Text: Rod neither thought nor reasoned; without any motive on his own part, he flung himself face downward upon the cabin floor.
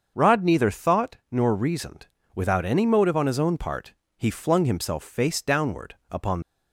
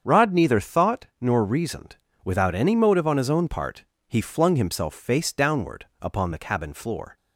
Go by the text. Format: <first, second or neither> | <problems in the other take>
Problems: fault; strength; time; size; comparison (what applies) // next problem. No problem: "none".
second | starts louder than the rest; until 1.1 s; 6.5 dB; strong in the second // stops before "the cabin floor"; at 6.4 s